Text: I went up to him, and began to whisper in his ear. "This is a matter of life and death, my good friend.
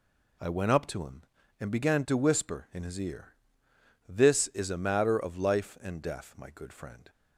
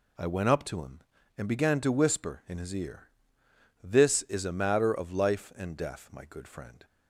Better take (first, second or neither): neither